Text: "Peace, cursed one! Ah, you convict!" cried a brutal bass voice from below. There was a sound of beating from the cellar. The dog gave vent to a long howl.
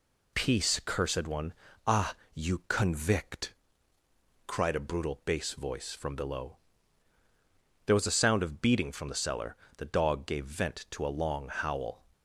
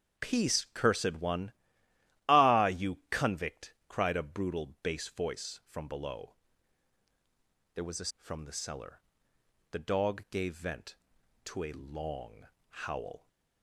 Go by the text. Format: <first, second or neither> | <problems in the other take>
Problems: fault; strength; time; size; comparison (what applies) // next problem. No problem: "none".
first | starts louder than the rest; strong; until 1.3 s; 7.5 dB // skips "sound of beating"; at 8.1 s // pauses between "long" and "howl"; slight; at 12.4 s; 0.22 s long